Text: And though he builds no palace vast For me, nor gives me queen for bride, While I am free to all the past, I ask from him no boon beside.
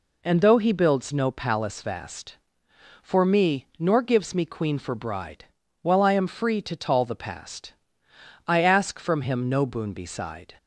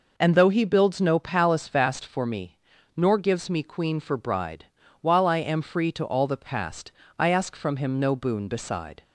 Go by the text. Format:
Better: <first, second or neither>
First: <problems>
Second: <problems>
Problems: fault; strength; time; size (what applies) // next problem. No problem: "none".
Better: second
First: says "tall" for "all"; at 6.7 s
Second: none